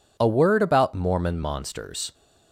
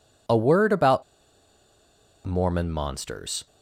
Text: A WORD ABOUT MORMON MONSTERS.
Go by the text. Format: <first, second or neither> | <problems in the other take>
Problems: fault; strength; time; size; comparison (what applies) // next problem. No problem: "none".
first | pauses between "ABOUT" and "MORMON"; at 1.0 s; 1.2 s long